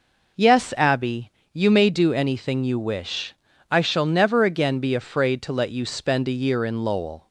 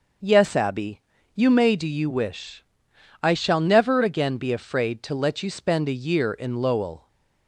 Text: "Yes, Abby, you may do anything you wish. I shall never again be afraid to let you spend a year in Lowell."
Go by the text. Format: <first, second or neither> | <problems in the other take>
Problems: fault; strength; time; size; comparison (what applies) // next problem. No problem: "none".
first | skips "anything"; at 1.8 s